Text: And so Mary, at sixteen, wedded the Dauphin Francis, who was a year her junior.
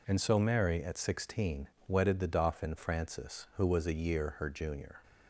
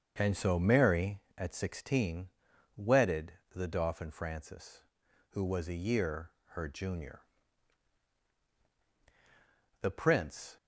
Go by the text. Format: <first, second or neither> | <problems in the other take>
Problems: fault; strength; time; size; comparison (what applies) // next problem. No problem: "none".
first | starts louder than the rest; until 1.1 s; 6.5 dB // pauses between "wedded" and "the"; slight; at 3.3 s; 0.22 s long // pauses between "year" and "her"; slight; at 6.3 s; 0.20 s long // goes on to say "The prince"; noticeable; from 9.8 s on; 0.76 s long